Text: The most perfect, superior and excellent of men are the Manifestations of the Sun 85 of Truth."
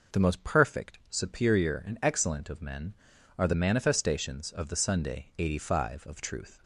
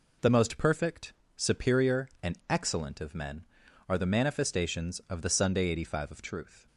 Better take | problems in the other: neither | none

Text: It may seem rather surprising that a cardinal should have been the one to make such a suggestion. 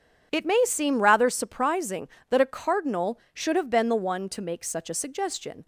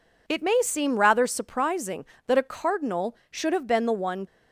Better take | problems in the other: first | stops before "to make such a suggestion"; at 4.2 s

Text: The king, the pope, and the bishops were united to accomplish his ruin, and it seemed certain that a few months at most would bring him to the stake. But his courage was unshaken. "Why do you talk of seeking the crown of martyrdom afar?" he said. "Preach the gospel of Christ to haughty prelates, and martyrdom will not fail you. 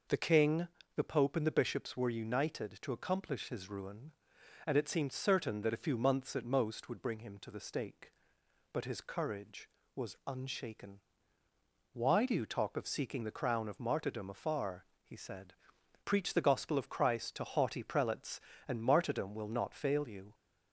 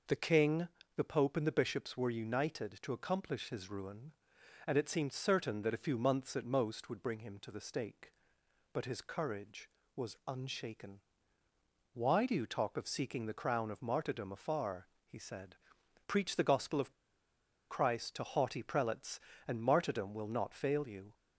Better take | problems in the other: first | pauses between "of" and "Christ"; noticeable; at 16.9 s; 0.78 s long

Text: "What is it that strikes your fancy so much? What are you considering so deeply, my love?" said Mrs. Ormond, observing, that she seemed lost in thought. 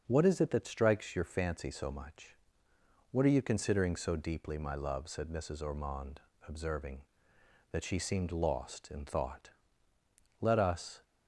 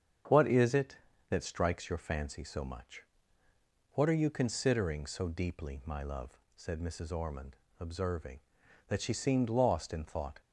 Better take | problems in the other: second | starts louder than the rest; until 1.0 s; 6.5 dB; strong in the second // goes on to say "Let us"; noticeable; from 10.4 s on; 0.62 s long

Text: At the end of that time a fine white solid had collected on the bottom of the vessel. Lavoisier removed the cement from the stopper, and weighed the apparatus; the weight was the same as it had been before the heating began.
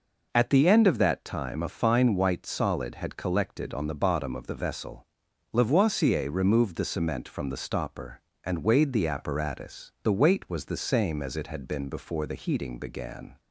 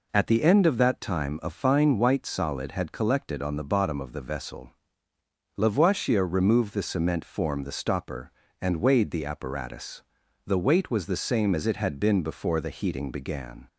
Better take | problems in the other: first | says "form" for "from"; at 7.2 s

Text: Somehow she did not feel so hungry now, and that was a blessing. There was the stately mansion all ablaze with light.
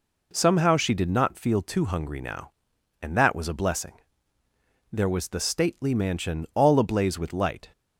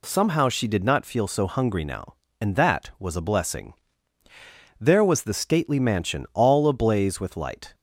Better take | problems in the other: second | says "too" for "so"; at 1.5 s

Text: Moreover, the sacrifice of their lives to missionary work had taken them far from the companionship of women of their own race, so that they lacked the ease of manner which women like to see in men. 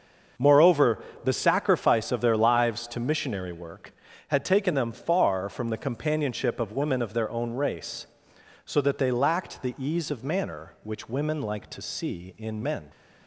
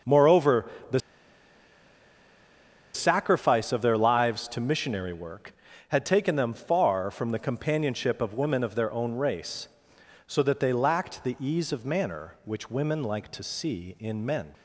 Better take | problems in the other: first | starts louder than the rest; until 3.2 s; 6.5 dB; also in the first // pauses between "the" and "sacrifice"; strong; at 0.9 s; 1.9 s long

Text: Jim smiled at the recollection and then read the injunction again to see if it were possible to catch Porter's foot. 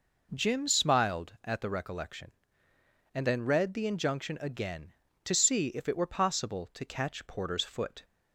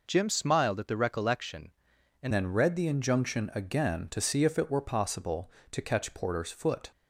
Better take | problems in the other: first | changes voice at "then"; from 2.3 s on; 4.6 s long

